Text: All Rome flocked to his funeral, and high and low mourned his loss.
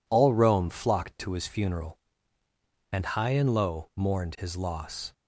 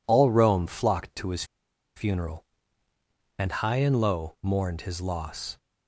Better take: first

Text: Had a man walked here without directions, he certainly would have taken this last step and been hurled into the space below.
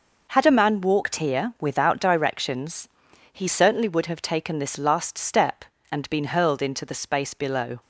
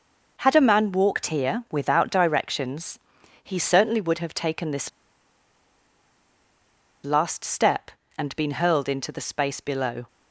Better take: first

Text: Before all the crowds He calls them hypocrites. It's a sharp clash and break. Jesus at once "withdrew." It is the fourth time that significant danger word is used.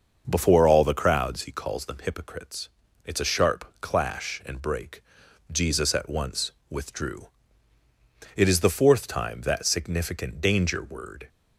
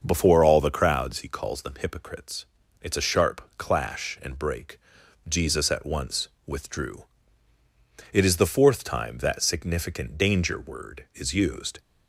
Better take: second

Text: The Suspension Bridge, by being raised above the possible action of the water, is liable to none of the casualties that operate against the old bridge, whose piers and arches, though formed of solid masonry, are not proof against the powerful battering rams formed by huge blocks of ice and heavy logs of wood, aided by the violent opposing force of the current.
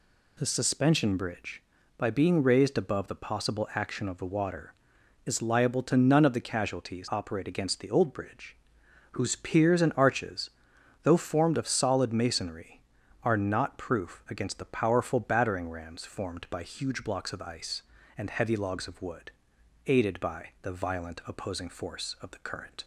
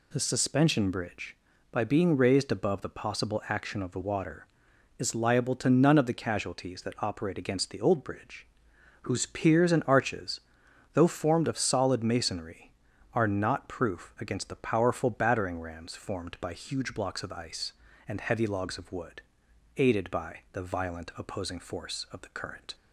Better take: second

